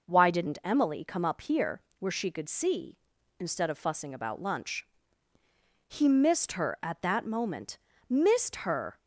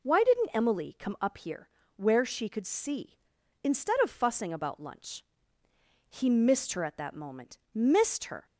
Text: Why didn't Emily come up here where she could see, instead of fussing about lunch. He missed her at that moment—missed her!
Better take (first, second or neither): neither